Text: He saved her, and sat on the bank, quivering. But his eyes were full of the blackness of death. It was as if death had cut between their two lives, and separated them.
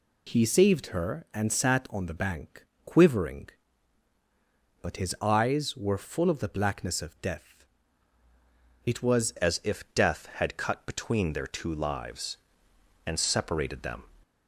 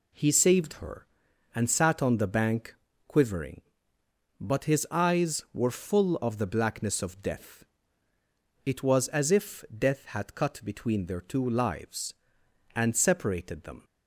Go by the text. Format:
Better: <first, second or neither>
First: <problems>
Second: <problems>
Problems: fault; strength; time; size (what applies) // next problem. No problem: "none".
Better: second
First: changes voice at "as"; from 9.3 s on; 4.7 s long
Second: none